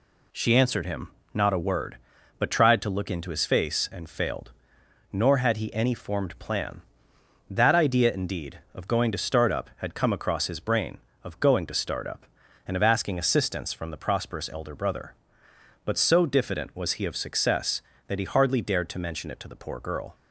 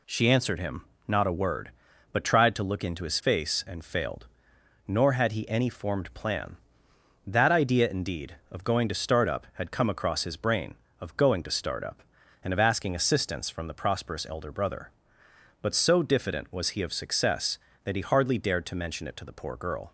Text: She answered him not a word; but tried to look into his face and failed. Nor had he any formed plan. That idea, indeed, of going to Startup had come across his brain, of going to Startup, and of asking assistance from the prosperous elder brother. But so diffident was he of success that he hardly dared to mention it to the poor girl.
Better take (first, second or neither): neither